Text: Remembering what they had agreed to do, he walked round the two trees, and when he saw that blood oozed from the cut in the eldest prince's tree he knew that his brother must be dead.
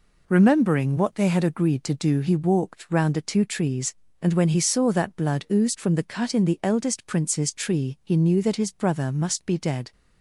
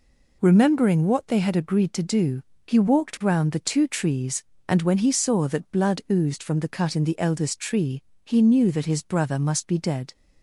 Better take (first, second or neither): first